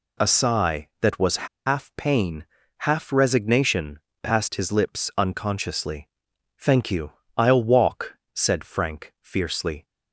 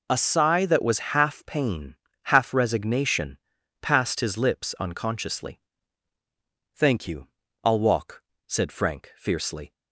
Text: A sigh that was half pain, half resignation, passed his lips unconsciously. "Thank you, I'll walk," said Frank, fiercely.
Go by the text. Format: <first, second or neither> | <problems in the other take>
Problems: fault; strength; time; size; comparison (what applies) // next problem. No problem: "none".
second | pauses between "was" and "half"; slight; at 1.4 s; 0.20 s long